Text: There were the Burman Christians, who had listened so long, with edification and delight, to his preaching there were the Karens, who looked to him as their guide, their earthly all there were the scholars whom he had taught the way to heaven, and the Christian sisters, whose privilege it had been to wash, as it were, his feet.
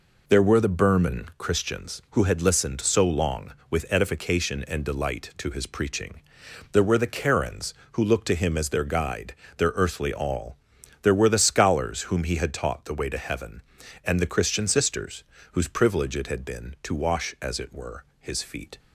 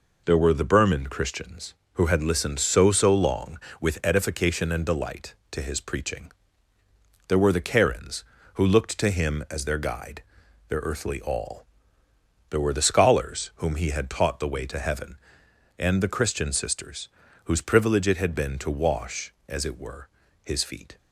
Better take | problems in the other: first | says "so" twice; at 2.9 s // pauses between "preaching" and "there"; noticeable; at 6.3 s; 0.96 s long; noticeable in the first // pauses between "all" and "there"; noticeable; at 11.6 s; 0.82 s long; noticeable in the first

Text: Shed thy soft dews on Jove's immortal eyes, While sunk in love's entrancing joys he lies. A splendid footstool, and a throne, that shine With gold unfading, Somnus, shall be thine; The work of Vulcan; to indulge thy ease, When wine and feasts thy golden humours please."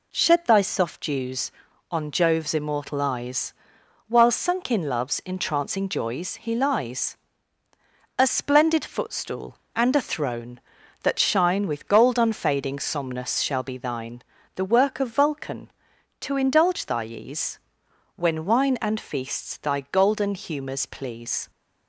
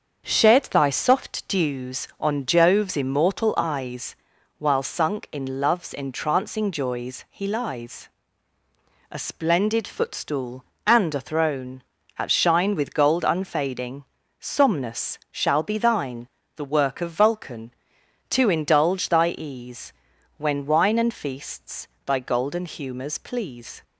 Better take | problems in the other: first | starts louder than the rest; until 1.3 s; 7 dB // says "at" for "that"; at 12.1 s // pauses between "feasts" and "thy"; slight; at 21.8 s; 0.20 s long

